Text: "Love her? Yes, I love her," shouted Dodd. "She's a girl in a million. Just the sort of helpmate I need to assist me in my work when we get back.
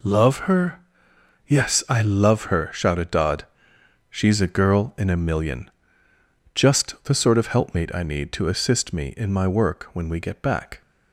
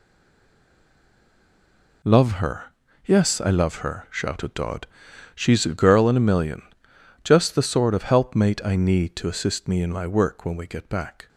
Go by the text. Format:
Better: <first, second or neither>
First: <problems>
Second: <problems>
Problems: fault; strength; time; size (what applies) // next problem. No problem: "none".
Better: first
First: none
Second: stays silent before the first word; noticeable; until 2.0 s; 2.0 s long